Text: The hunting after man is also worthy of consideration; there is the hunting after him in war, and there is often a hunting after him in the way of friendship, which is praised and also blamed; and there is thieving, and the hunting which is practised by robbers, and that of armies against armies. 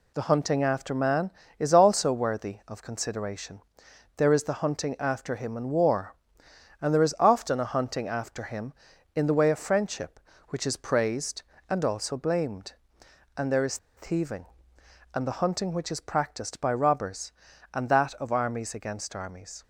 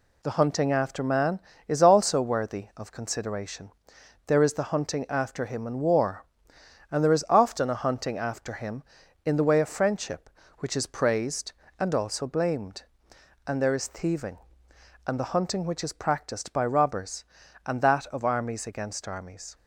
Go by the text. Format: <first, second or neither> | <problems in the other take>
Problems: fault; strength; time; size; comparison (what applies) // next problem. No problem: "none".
second | pauses between "is" and "thieving"; slight; at 13.7 s; 0.19 s long